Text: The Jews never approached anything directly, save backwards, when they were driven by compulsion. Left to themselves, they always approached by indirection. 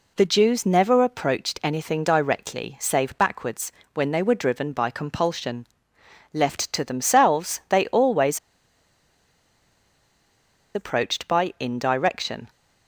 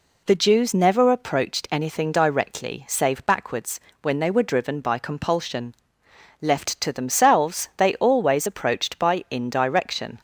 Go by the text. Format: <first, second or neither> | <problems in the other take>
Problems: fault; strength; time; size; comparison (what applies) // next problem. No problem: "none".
second | pauses between "always" and "approached"; strong; at 8.3 s; 2.3 s long